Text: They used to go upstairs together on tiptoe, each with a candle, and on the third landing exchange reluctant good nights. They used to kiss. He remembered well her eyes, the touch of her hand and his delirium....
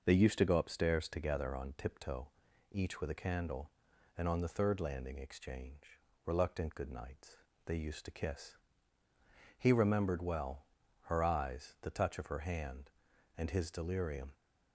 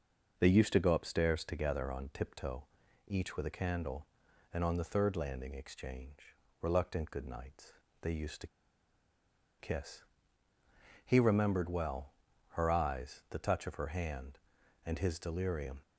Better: first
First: pauses between "exchange" and "reluctant"; slight; at 5.9 s; 0.28 s long // pauses between "well" and "her"; at 10.6 s; 0.40 s long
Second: pauses between "exchange" and "reluctant"; slight; at 6.3 s; 0.28 s long // pauses between "to" and "kiss"; at 8.4 s; 1.1 s long // pauses between "well" and "her"; at 12.1 s; 0.40 s long

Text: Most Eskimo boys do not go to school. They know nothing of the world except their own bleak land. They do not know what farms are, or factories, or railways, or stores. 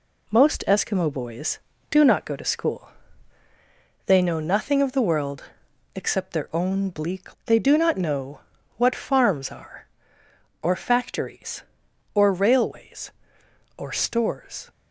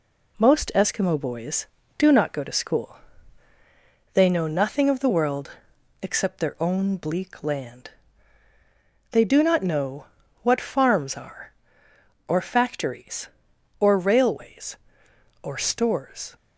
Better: second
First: pauses between "world" and "except"; noticeable; at 5.4 s; 0.50 s long // skips "land"; at 7.4 s // pauses between "know" and "what"; slight; at 8.4 s; 0.36 s long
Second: pauses between "world" and "except"; noticeable; at 5.5 s; 0.50 s long // pauses between "know" and "what"; slight; at 10.0 s; 0.36 s long

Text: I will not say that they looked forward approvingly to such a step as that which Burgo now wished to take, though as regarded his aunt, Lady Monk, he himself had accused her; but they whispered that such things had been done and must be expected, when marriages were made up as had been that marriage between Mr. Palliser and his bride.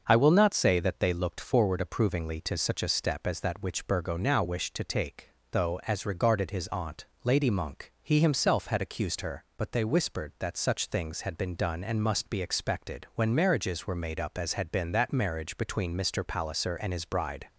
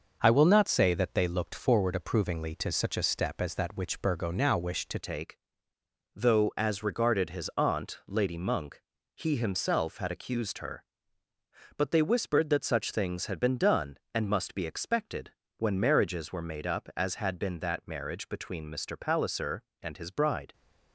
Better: first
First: starts louder than the rest; until 1.0 s; 6.5 dB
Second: starts louder than the rest; noticeable; until 1.2 s; 6 dB // changes voice at "take"; from 5.0 s on; 15.5 s long

